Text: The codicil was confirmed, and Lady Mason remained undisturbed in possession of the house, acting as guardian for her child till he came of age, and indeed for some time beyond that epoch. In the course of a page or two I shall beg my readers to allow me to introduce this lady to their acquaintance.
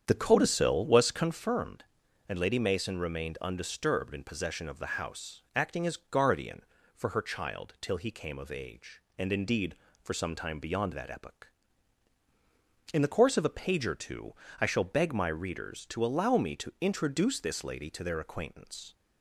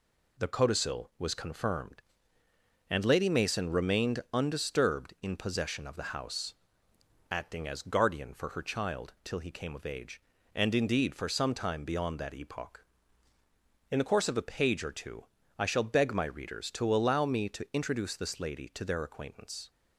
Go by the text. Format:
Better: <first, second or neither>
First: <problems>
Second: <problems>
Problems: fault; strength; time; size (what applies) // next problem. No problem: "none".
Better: second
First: starts louder than the rest; strong; until 1.5 s; 8 dB // pauses between "two" and "I"; slight; at 14.3 s; 0.28 s long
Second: pauses between "two" and "I"; slight; at 15.2 s; 0.34 s long